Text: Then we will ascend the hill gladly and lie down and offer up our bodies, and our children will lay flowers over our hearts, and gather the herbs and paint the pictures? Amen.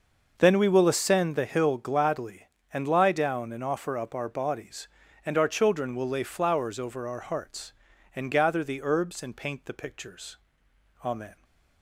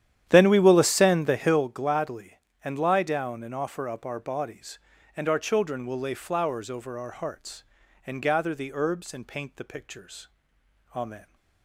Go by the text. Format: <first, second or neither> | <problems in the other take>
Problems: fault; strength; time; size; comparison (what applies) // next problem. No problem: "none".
first | starts louder than the rest; strong; until 1.6 s; 10.5 dB